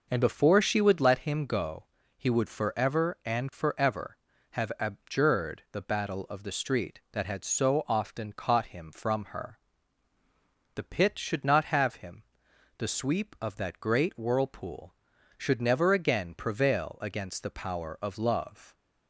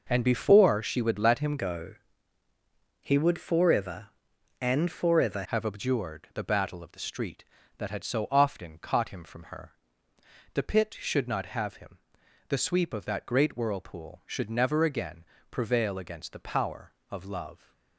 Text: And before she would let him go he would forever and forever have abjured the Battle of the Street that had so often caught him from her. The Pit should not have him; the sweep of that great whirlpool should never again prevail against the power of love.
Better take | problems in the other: first | changes voice from "go" to "forever"; from 1.5 to 5.4 s; 3.9 s long // pauses between "go" and "he"; at 1.9 s; 1.0 s long; slight in the first // pauses between "again" and "prevail"; slight; at 15.2 s; 0.26 s long

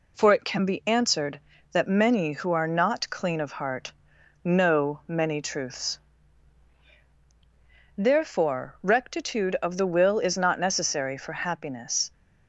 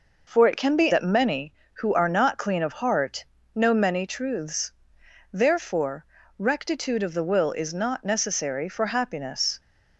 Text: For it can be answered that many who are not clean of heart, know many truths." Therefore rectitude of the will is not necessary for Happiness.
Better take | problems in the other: first | skips "answered"; at 0.9 s // pauses between "Therefore" and "rectitude"; slight; at 6.0 s; 0.34 s long

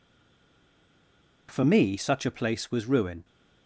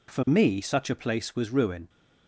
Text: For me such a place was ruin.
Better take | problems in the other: second | stays silent before the first word; noticeable; until 1.4 s; 1.4 s long

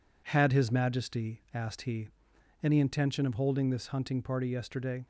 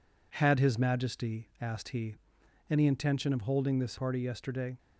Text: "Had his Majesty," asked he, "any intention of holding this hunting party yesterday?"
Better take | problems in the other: first | skips "hunting"; at 3.9 s

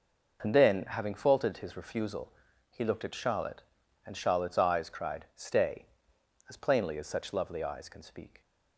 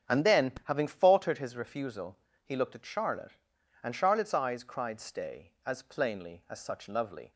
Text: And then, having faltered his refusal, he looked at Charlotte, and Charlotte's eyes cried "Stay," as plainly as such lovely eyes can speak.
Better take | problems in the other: first | starts louder than the rest; strong; until 1.2 s; 8 dB // stops before "eyes can speak"; at 7.3 s

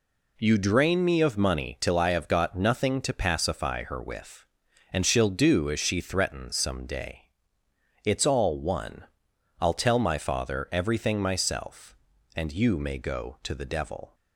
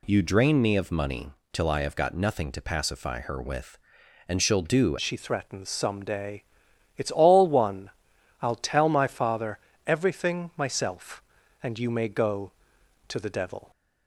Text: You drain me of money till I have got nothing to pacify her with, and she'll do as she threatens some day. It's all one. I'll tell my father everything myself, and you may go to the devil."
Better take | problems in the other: first | pauses between "money" and "till"; slight; at 1.3 s; 0.22 s long // changes voice at "as"; from 4.9 s on; 8.8 s long // pauses between "father" and "everything"; slight; at 9.5 s; 0.28 s long

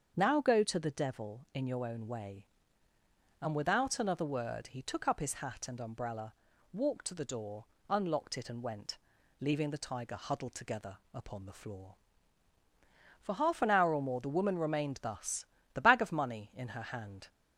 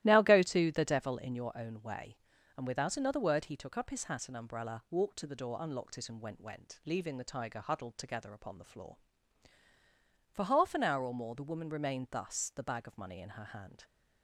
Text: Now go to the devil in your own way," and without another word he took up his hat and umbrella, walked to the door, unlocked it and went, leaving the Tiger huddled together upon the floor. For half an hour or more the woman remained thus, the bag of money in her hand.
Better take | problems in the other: first | starts louder than the rest; strong; until 1.0 s; 14.5 dB; strong in the first // says "went" twice; at 6.4 s

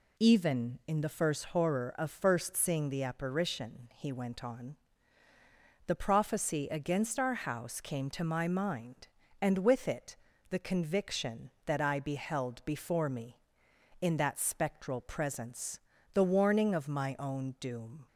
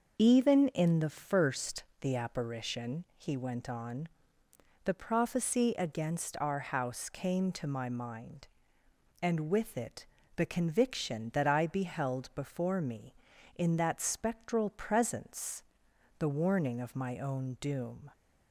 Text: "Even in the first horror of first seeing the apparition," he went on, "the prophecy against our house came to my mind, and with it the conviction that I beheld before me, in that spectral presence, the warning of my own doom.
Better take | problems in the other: first | starts louder than the rest; noticeable; until 1.2 s; 6 dB // skips "horror of first seeing"; at 1.9 s // pauses between "it" and "the"; slight; at 10.0 s; 0.30 s long; slight in the first

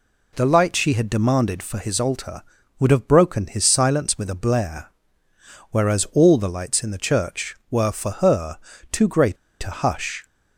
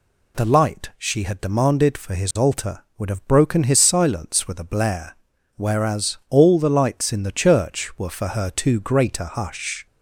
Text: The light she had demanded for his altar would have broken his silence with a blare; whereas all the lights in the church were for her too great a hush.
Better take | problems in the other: second | pauses between "her" and "too"; slight; at 8.5 s; 0.32 s long // pauses between "great" and "a"; slight; at 9.3 s; 0.28 s long

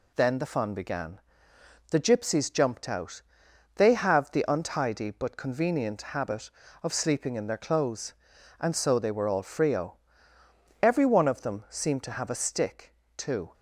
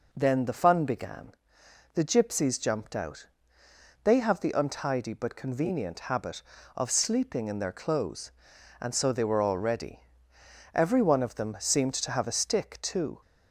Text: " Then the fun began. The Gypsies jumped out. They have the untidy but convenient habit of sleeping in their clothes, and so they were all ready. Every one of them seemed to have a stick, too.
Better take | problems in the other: second | says "frio" for "ready"; at 9.4 s

